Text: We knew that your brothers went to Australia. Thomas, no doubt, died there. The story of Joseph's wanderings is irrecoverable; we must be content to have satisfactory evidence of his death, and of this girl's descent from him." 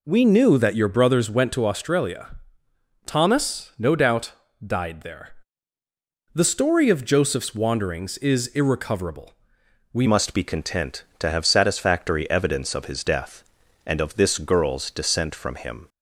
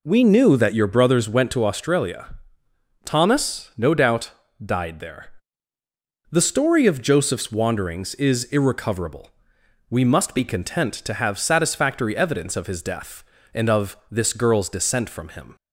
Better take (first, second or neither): second